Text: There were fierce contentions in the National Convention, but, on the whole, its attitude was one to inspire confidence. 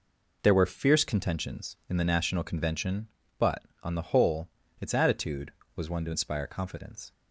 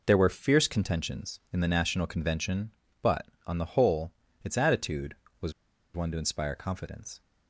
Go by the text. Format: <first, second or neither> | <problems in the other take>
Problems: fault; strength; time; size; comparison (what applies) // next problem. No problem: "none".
first | pauses between "was" and "one"; at 5.5 s; 0.43 s long